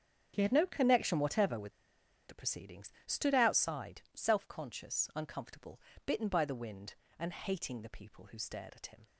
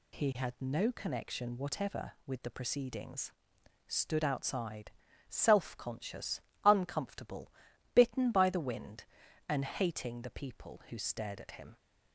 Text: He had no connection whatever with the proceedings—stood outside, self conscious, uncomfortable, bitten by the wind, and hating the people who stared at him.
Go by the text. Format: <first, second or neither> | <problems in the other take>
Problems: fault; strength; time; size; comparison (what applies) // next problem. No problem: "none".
second | starts louder than the rest; strong; until 1.3 s; 7.5 dB // pauses between "with" and "the"; noticeable; at 1.7 s; 0.57 s long